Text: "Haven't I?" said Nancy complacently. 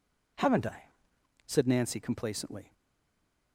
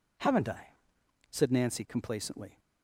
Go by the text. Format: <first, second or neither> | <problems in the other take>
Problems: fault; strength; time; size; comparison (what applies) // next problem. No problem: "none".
second | stays silent after the last word; slight; from 2.7 s on; 0.8 s long